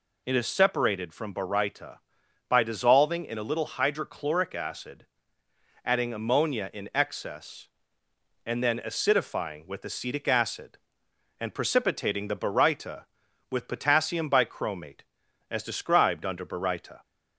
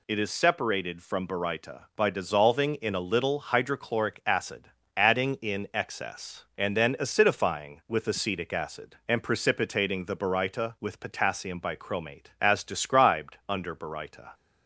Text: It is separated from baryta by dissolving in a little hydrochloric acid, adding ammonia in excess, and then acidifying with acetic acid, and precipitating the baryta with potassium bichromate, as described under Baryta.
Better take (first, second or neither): first